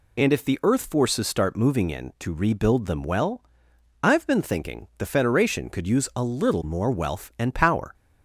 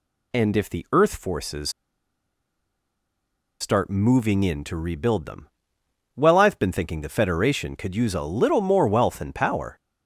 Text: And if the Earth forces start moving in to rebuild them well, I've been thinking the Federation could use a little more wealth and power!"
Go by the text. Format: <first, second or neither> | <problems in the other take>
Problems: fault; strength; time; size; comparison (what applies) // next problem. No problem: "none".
first | pauses between "forces" and "start"; strong; at 1.6 s; 1.9 s long // pauses between "them" and "well"; noticeable; at 5.4 s; 0.68 s long